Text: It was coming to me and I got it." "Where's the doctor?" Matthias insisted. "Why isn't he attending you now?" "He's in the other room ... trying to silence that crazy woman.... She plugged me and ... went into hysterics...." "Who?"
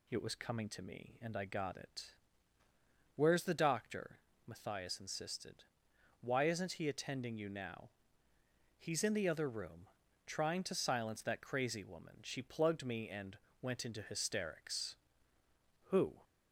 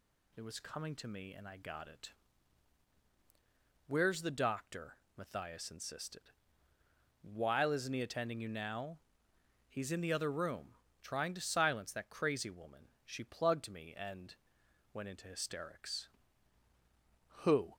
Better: first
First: none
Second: says "While" for "Why"; at 7.2 s

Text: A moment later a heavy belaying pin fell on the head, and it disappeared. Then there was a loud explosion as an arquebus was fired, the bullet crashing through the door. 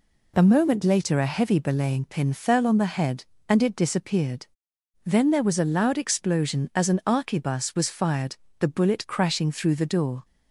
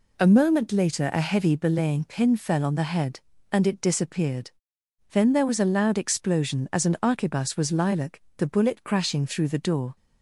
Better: first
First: none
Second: says "lilac" for "fired"; at 7.7 s

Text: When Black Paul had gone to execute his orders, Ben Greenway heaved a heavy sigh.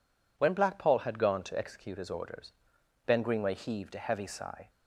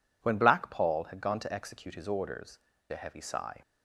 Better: first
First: none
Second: skips "Ben Greenway heaved"; at 2.7 s

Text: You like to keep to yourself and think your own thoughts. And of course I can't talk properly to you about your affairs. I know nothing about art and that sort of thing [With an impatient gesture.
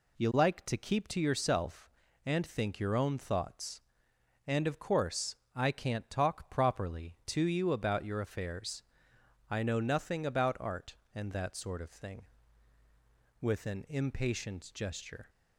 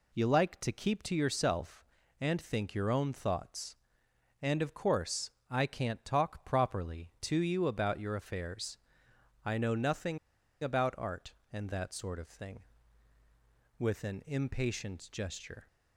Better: first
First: pauses between "course" and "I"; slight; at 5.3 s; 0.20 s long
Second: pauses between "course" and "I"; slight; at 5.2 s; 0.20 s long // pauses between "nothing" and "about"; at 10.1 s; 0.44 s long

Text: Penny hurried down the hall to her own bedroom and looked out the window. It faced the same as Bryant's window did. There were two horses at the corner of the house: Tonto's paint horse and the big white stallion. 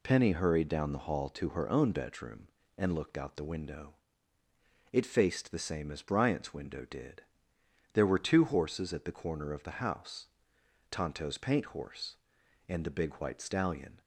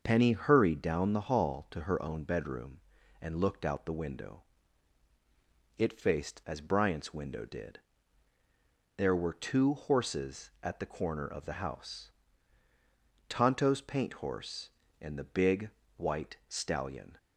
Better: first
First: none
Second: starts louder than the rest; until 1.0 s; 6 dB // skips "the same"; at 6.4 s // pauses between "big" and "white"; slight; at 15.7 s; 0.24 s long

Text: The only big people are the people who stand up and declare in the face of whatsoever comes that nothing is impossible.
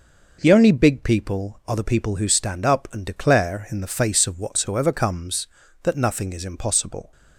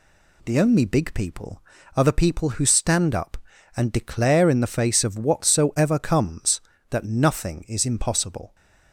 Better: neither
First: none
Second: none

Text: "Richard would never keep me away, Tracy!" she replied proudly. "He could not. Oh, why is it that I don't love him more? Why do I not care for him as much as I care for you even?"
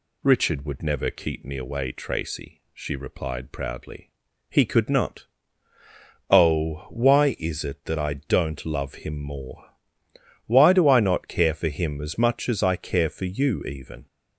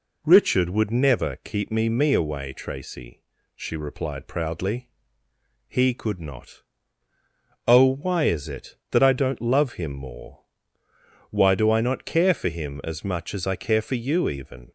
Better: first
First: none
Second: says "me" twice; at 1.8 s

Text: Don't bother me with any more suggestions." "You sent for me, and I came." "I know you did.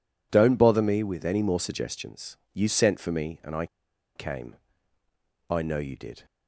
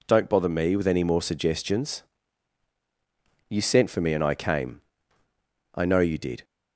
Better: second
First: pauses between "I" and "came"; noticeable; at 3.6 s; 0.49 s long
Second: none

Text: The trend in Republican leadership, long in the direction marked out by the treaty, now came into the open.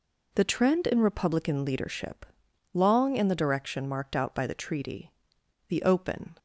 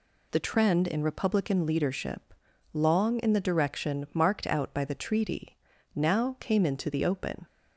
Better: second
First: skips "now came into"; at 5.3 s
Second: none

